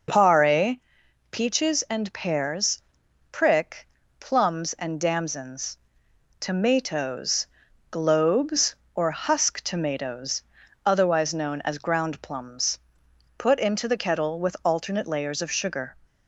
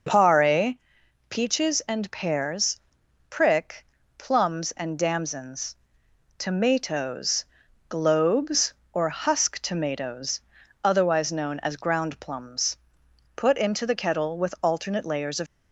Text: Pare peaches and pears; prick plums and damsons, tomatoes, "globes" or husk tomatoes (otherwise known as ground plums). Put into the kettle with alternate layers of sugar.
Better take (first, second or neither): first